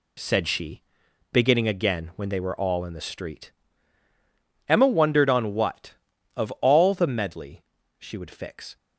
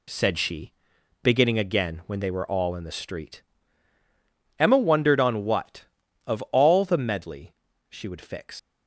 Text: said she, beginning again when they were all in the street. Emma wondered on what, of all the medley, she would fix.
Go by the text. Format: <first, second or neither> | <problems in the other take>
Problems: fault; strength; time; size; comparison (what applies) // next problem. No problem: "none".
first | leaves "fix" unfinished; at 8.5 s; 70 ms